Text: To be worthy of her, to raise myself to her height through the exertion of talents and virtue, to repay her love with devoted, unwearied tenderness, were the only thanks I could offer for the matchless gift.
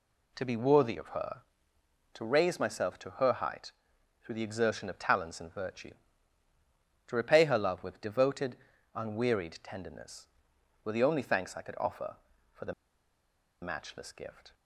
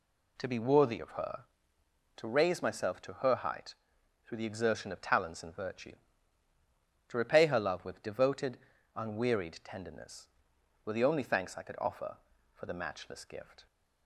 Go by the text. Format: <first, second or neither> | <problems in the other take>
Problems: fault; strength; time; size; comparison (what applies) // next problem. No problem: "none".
second | pauses between "height" and "through"; noticeable; at 3.7 s; 0.52 s long; noticeable in the second // pauses between "the" and "matchless"; noticeable; at 12.7 s; 0.88 s long